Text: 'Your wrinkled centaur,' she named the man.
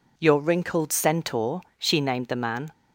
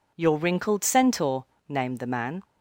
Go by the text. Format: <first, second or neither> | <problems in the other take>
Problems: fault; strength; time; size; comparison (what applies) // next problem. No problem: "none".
first | skips "she"; at 1.5 s